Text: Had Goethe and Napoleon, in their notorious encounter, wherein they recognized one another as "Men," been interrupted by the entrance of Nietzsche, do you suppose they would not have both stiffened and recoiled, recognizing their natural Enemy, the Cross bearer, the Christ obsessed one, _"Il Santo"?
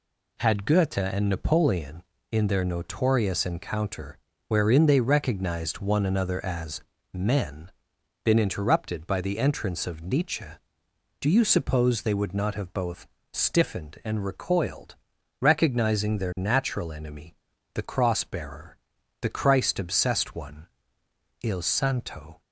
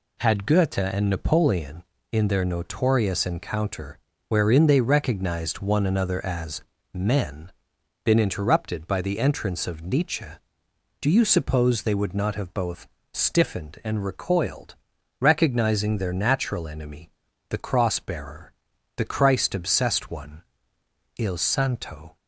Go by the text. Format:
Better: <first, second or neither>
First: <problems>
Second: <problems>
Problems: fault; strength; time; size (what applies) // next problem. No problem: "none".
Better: neither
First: pauses between "as" and "Men"; slight; at 6.8 s; 0.32 s long // pauses between "both" and "stiffened"; slight; at 13.0 s; 0.24 s long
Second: pauses between "as" and "Men"; slight; at 6.6 s; 0.32 s long // pauses between "both" and "stiffened"; slight; at 12.8 s; 0.24 s long